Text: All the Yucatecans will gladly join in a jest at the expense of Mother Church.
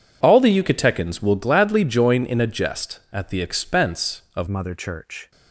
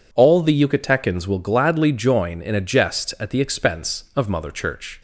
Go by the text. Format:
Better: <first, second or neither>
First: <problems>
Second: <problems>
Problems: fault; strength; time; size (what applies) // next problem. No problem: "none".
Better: second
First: changes voice at "Mother"; from 4.4 s on; 0.9 s long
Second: none